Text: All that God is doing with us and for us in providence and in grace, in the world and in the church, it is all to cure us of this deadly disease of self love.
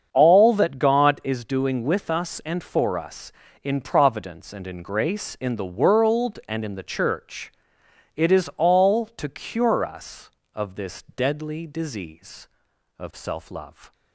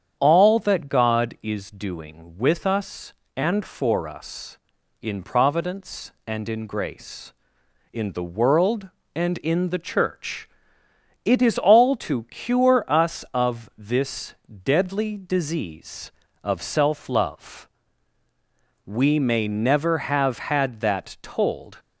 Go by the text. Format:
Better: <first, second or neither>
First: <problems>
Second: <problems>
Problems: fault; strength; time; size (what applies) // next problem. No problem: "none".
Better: first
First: starts louder than the rest; strong; until 1.1 s; 7 dB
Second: starts louder than the rest; strong; until 1.1 s; 8.5 dB // pauses between "this" and "deadly"; slight; at 14.3 s; 0.30 s long // goes on to say "We may never have had that told"; strong; from 18.8 s on; 2.9 s long